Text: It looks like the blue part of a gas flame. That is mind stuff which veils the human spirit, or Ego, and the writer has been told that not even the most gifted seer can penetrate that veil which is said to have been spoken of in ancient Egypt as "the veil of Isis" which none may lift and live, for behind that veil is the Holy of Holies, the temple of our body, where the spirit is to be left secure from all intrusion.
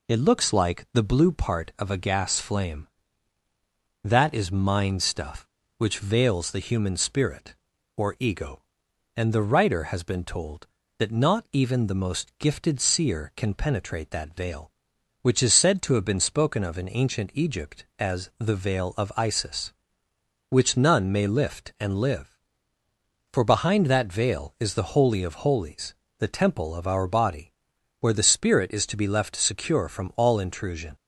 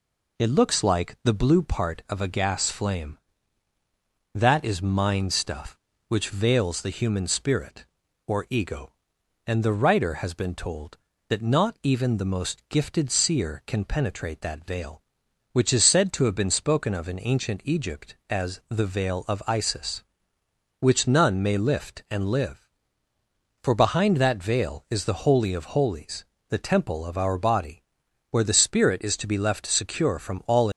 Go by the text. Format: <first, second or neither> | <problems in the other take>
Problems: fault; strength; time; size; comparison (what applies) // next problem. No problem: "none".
first | stops before "intrusion"; at 30.7 s